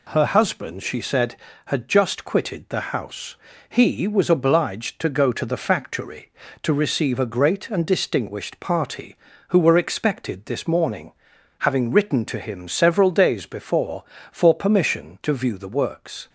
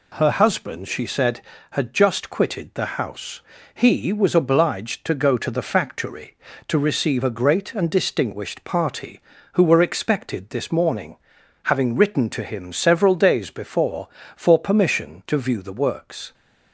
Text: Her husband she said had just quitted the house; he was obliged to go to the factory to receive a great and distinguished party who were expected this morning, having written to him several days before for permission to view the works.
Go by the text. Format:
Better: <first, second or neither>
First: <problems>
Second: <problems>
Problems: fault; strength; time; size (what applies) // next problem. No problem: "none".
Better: neither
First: none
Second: none